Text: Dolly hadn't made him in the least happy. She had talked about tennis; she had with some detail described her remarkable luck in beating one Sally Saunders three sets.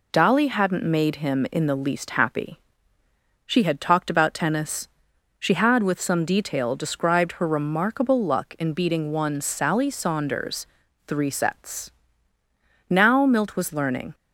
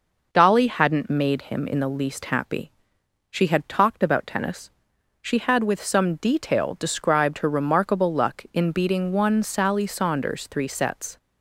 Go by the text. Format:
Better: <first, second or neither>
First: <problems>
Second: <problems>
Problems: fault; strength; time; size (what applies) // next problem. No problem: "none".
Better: second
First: pauses between "Saunders" and "three"; at 10.6 s; 0.40 s long // goes on to say "Now Milt was learning"; noticeable; from 12.8 s on; 1.2 s long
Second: none